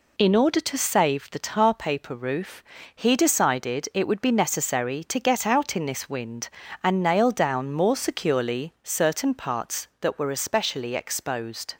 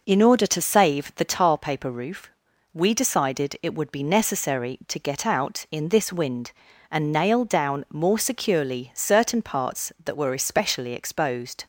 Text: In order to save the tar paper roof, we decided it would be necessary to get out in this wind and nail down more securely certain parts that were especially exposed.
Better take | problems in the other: second | says "he" for "we"; at 2.9 s

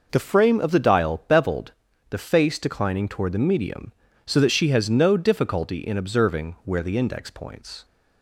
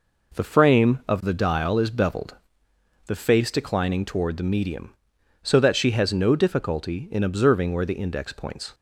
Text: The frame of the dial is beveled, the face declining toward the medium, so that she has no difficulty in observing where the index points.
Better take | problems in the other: second | skips "is"; at 1.2 s

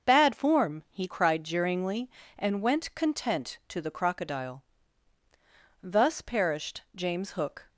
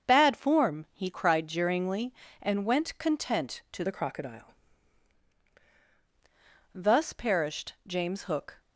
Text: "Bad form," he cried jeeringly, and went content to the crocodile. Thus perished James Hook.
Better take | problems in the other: first | starts louder than the rest; until 1.1 s; 7 dB; also in the first // changes voice from "the" to "crocodile"; from 3.8 to 4.5 s; 0.7 s long

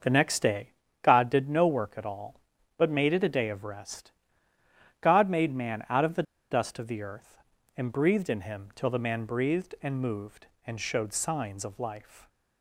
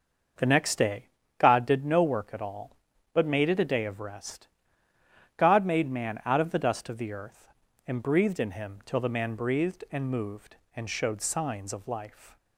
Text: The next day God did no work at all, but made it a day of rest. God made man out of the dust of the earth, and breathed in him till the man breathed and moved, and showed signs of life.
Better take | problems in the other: second | starts louder than the rest; until 1.3 s; 6.5 dB; also in the second // pauses between "day" and "God"; slight; at 0.7 s; 0.32 s long; slight in the second // pauses between "the" and "dust"; slight; at 6.2 s; 0.28 s long

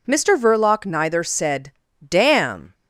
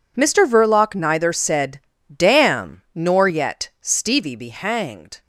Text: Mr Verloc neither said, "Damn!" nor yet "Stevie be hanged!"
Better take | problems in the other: second | stops before "nor yet Stevie be hanged"; at 2.7 s

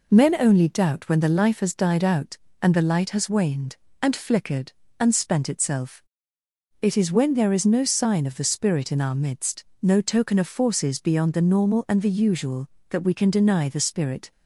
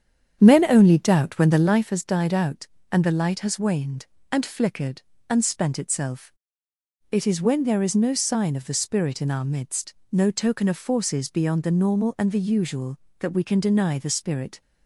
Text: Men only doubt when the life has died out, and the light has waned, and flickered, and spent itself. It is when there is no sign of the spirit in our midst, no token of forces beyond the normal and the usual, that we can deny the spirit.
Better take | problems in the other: first | starts louder than the rest; strong; until 1.9 s; 8.5 dB

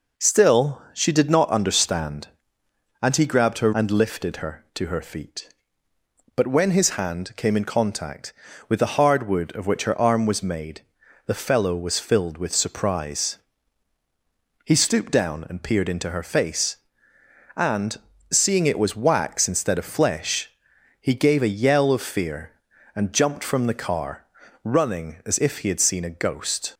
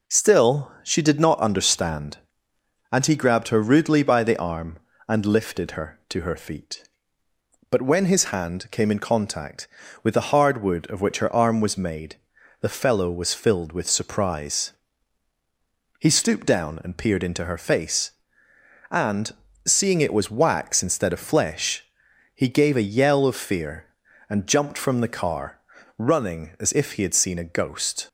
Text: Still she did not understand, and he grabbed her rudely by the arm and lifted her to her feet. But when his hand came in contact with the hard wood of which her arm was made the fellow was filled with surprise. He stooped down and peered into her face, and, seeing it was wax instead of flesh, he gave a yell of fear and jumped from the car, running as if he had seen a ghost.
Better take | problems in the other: second | skips "rudely by the arm"; at 3.7 s // pauses between "made" and "the"; noticeable; at 10.8 s; 0.46 s long; noticeable in the second

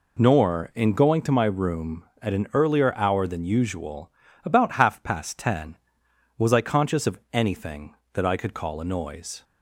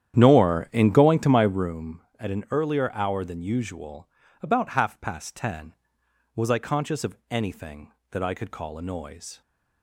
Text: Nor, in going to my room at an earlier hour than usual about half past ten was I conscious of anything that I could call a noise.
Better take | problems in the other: first | starts louder than the rest; strong; until 1.7 s; 10 dB // pauses between "usual" and "about"; slight; at 4.0 s; 0.34 s long; slight in the first

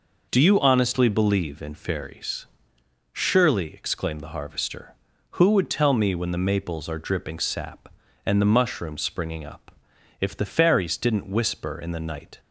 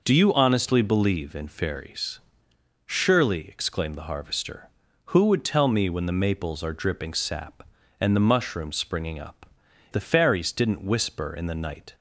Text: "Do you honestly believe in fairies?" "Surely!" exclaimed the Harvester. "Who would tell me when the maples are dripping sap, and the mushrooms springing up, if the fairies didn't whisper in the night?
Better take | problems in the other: first | skips "if"; at 9.6 s

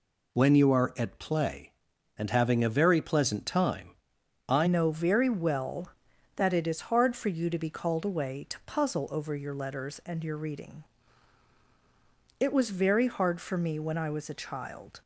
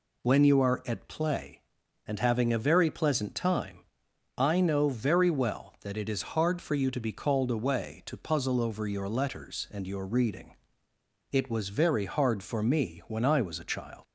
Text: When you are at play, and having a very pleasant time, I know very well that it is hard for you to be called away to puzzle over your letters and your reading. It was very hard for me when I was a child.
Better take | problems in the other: second | changes voice at "know"; from 4.6 s on; 10.4 s long

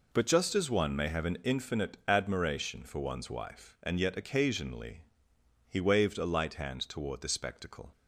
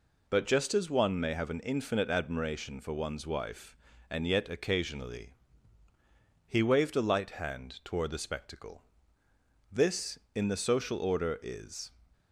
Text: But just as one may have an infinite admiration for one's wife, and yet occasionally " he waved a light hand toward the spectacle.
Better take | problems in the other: first | goes on to say "This in the social order is"; strong; from 9.7 s on; 2.2 s long

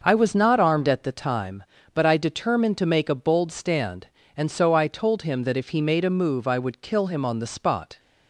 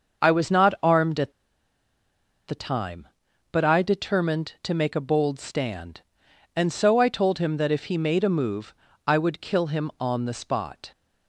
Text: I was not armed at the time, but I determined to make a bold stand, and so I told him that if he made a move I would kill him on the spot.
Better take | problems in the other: first | starts louder than the rest; until 1.3 s; 6.5 dB; noticeable in the first // pauses between "at" and "the"; at 1.3 s; 1.1 s long // pauses between "move" and "I"; slight; at 8.7 s; 0.34 s long

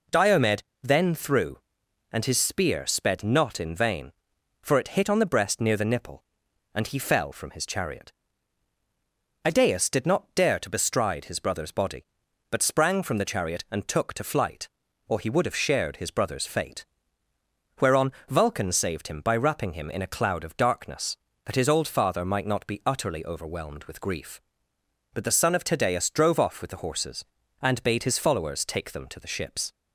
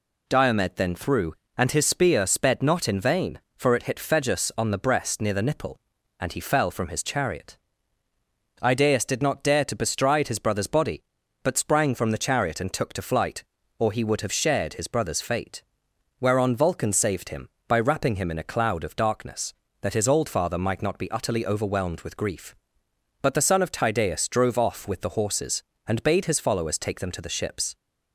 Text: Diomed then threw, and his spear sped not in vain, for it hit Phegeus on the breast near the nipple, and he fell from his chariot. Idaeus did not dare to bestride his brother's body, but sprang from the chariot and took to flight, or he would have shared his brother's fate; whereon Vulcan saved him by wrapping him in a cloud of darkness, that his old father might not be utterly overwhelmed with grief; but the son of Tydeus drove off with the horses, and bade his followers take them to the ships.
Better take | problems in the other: second | pauses between "Diomed" and "then"; slight; at 0.6 s; 0.20 s long // skips "Phegeus"; at 5.0 s // pauses between "whereon" and "Vulcan"; slight; at 18.1 s; 0.16 s long

